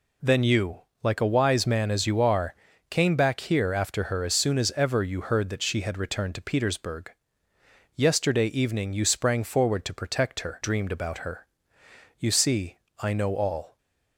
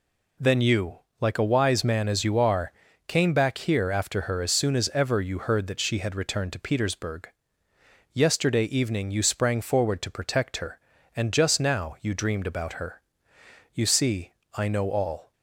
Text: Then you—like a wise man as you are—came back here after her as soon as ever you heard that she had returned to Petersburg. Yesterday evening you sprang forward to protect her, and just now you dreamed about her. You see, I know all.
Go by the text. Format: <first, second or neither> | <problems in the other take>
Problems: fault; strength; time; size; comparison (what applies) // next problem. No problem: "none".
second | skips "and just now you"; at 10.6 s